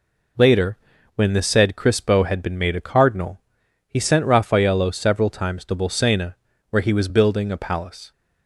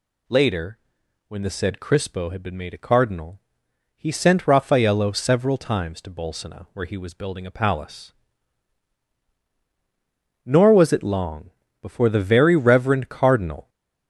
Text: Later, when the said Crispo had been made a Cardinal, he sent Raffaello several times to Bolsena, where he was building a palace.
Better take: first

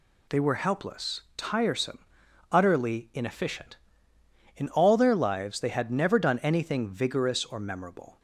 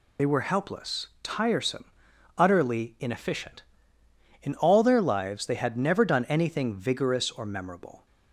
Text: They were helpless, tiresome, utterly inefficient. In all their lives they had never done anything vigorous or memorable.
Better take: first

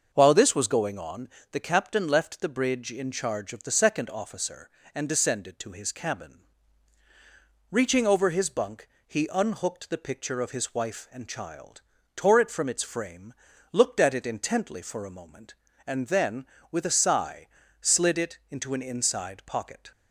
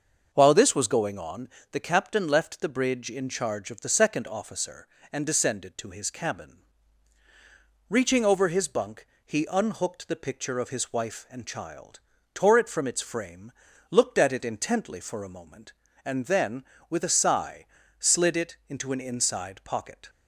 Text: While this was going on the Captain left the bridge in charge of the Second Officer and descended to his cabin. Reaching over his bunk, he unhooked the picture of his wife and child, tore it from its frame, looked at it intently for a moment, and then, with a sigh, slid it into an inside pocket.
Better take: neither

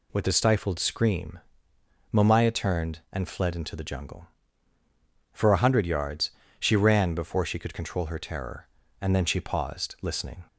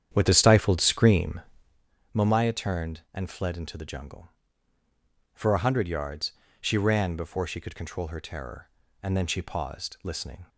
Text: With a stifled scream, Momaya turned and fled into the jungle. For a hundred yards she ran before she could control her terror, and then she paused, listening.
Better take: first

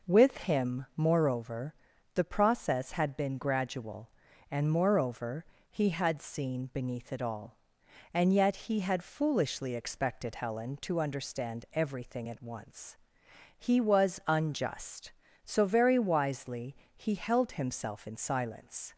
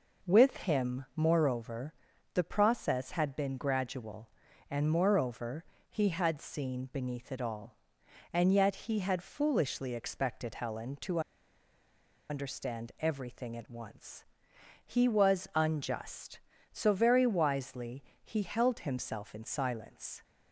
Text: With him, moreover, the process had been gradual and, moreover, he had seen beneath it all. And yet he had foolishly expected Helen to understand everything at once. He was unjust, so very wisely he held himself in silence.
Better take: first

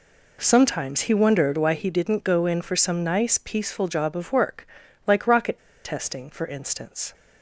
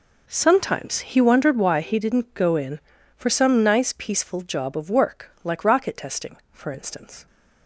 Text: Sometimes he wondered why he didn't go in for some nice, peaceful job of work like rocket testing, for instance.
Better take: second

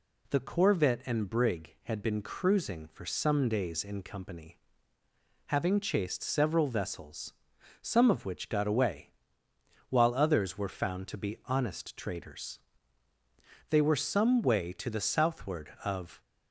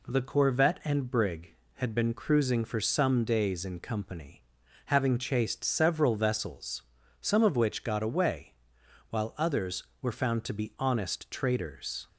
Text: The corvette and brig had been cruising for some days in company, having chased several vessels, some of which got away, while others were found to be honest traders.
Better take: second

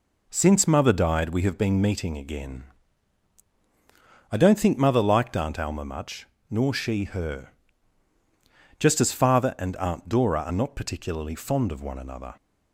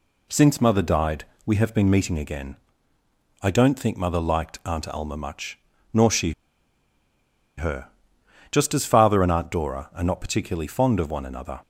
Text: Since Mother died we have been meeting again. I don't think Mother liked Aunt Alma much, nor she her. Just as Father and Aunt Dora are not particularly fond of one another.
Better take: first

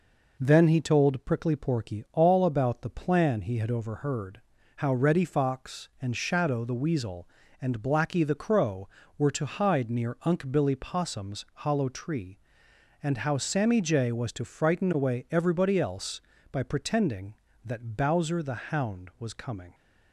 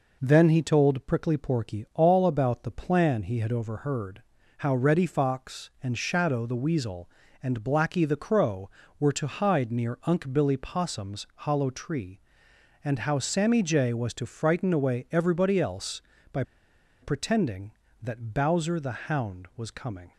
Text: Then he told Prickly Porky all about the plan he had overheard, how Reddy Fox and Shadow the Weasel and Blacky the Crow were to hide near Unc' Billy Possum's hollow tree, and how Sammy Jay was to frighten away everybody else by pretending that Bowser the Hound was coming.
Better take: first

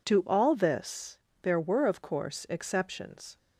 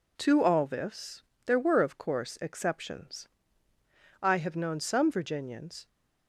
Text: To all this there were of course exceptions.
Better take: first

